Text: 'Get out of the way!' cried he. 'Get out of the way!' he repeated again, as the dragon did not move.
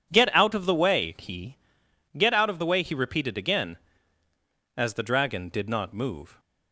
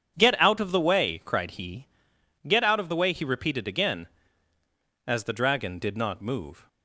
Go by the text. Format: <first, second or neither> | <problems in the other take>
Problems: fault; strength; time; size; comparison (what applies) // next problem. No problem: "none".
second | skips "cried"; at 1.1 s